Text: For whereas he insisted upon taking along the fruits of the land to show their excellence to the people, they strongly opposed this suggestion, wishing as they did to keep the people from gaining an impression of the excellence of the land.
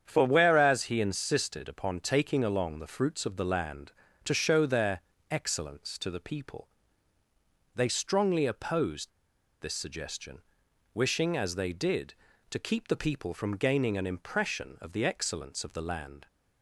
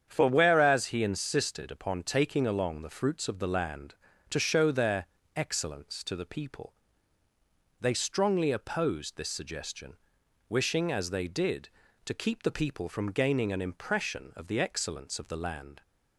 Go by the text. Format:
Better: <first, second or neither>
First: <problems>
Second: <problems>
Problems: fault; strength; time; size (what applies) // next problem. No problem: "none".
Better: second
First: starts louder than the rest; strong; until 1.0 s; 8 dB // pauses between "their" and "excellence"; slight; at 5.0 s; 0.30 s long // pauses between "opposed" and "this"; noticeable; at 9.1 s; 0.50 s long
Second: starts louder than the rest; strong; until 1.0 s; 8 dB // pauses between "their" and "excellence"; slight; at 5.0 s; 0.30 s long